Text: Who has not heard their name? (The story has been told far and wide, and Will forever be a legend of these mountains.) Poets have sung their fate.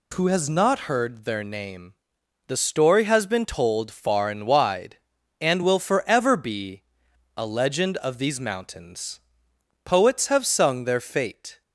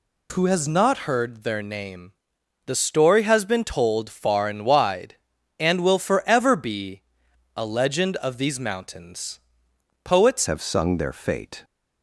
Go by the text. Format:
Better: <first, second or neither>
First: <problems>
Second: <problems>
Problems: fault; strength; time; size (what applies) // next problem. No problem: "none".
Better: first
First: pauses between "be" and "a"; noticeable; at 6.8 s; 0.56 s long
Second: pauses between "be" and "a"; noticeable; at 7.0 s; 0.56 s long // changes voice at "have"; from 10.4 s on; 1.2 s long